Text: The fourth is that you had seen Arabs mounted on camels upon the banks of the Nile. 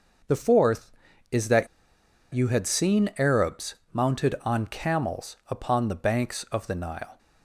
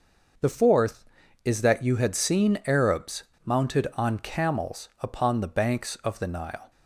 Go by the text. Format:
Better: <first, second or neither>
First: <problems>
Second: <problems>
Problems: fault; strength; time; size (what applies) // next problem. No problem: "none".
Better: second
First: starts louder than the rest; noticeable; until 2.3 s; 6 dB // pauses between "that" and "you"; noticeable; at 1.6 s; 0.66 s long // pauses between "Arabs" and "mounted"; slight; at 3.7 s; 0.18 s long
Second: starts louder than the rest; until 1.8 s; 6 dB // pauses between "Arabs" and "mounted"; slight; at 3.2 s; 0.21 s long